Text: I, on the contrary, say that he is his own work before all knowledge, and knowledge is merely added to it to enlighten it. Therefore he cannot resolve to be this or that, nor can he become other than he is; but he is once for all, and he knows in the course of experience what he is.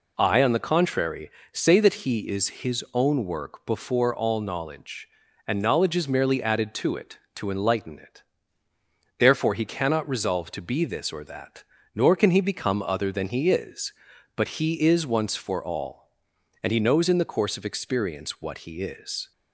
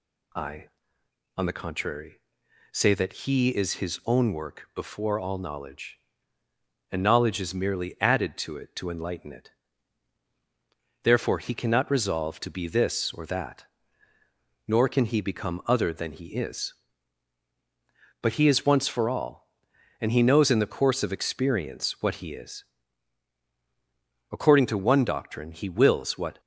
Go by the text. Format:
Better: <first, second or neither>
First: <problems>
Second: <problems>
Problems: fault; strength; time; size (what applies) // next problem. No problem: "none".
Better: first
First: none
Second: goes on to say "According to one doctrine he wills what"; strong; from 24.2 s on; 2.1 s long